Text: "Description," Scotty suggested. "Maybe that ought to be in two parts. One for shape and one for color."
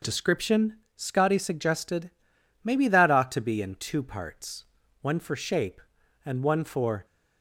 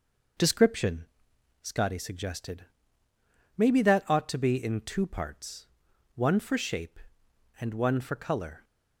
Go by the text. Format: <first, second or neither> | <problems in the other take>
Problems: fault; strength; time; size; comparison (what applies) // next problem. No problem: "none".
second | stops before "color"; at 7.0 s